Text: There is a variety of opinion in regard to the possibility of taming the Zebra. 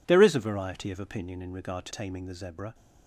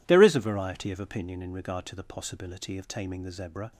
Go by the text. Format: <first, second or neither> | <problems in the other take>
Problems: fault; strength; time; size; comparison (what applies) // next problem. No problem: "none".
second | skips "the possibility of"; at 1.9 s